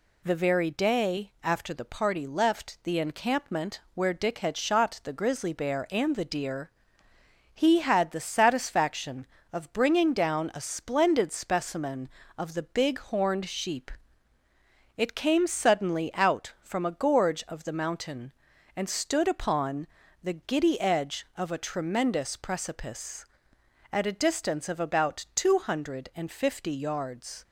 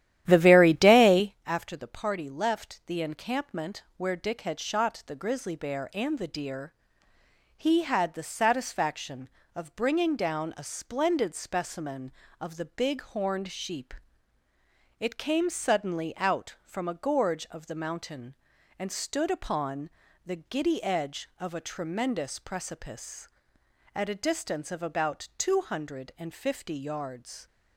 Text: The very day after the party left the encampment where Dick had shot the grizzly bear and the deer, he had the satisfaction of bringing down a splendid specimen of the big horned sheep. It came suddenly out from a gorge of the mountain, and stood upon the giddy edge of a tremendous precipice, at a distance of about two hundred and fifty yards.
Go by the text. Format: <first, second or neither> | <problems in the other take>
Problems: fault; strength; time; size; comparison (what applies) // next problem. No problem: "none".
first | starts louder than the rest; strong; until 1.4 s; 12 dB // pauses between "upon" and "the"; slight; at 19.9 s; 0.36 s long; slight in the first